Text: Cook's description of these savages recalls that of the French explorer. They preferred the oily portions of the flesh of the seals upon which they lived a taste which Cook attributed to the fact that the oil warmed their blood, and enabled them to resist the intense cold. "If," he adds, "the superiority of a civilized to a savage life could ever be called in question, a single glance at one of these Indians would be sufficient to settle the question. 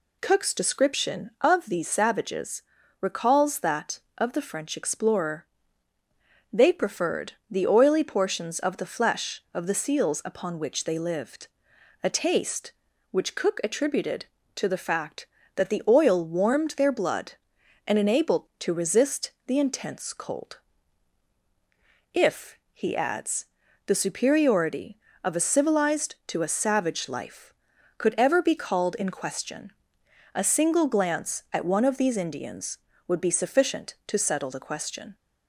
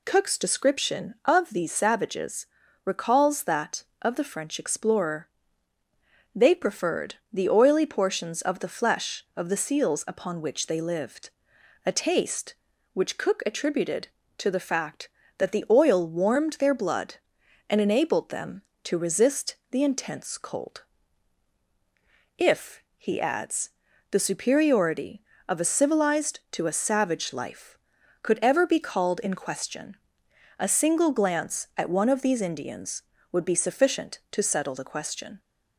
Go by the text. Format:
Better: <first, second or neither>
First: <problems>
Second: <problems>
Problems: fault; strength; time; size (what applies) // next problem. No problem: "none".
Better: second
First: pauses between "savages" and "recalls"; at 2.6 s; 0.38 s long // pauses between "preferred" and "the"; slight; at 7.3 s; 0.18 s long // pauses between "lived" and "a"; noticeable; at 11.4 s; 0.56 s long // skips "them"; at 18.5 s // pauses between "resist" and "the"; slight; at 19.3 s; 0.16 s long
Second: pauses between "savages" and "recalls"; at 2.4 s; 0.38 s long // pauses between "preferred" and "the"; slight; at 7.1 s; 0.18 s long // pauses between "lived" and "a"; noticeable; at 11.2 s; 0.56 s long // pauses between "resist" and "the"; slight; at 19.5 s; 0.16 s long